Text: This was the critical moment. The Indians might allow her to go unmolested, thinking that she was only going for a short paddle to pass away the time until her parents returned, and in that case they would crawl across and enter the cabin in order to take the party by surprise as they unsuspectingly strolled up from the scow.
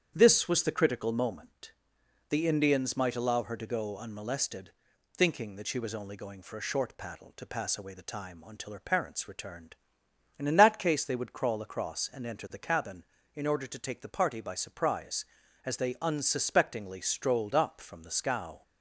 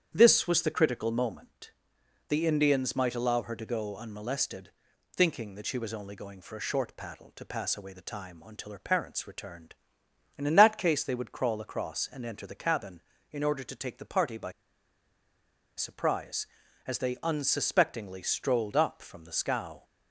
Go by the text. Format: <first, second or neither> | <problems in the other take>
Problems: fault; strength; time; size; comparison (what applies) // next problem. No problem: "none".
first | starts louder than the rest; strong; until 1.1 s; 8.5 dB; strong in the first // pauses between "by" and "surprise"; strong; at 14.5 s; 1.2 s long